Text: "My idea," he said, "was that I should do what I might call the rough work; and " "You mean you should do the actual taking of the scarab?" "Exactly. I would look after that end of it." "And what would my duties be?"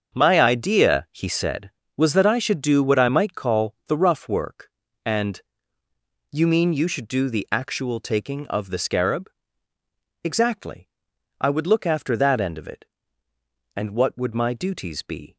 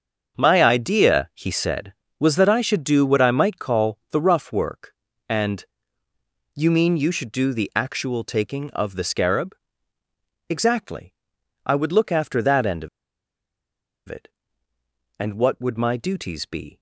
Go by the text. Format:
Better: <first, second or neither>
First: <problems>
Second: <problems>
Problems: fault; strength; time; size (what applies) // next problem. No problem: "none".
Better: first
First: starts louder than the rest; strong; until 1.1 s; 7.5 dB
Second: starts louder than the rest; strong; until 1.4 s; 7.5 dB // pauses between "of" and "it"; at 12.8 s; 1.2 s long